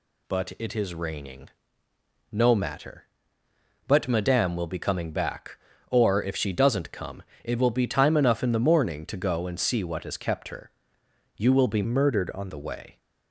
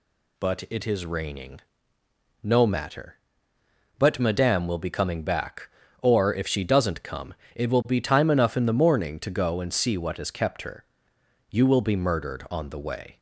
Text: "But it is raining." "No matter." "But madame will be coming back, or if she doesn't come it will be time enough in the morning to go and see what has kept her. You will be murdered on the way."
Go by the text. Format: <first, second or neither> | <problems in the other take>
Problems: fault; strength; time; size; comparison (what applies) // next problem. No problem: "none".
second | pauses between "come" and "it"; slight; at 7.2 s; 0.22 s long; slight in the second // changes voice from "murdered" to "on"; from 11.8 to 12.4 s; 0.6 s long